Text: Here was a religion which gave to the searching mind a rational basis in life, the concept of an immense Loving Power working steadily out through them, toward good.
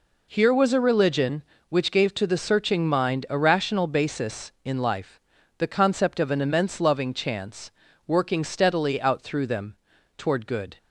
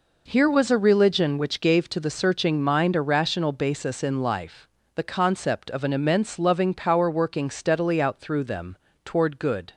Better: second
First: says "Chance" for "Power"; at 7.1 s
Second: none

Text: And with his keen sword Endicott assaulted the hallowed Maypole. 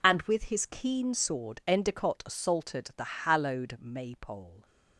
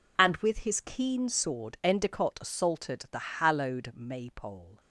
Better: neither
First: none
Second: none

